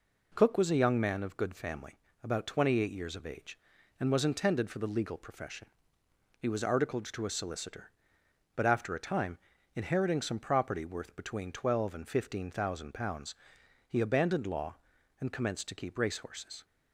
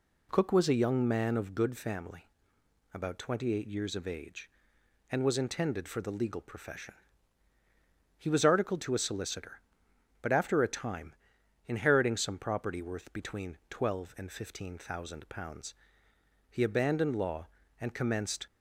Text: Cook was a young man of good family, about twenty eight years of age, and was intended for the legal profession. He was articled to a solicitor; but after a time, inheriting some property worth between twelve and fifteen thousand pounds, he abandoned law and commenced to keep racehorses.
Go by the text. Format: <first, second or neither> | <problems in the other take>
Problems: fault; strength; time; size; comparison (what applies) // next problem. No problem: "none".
first | stops before "to keep racehorses"; at 18.4 s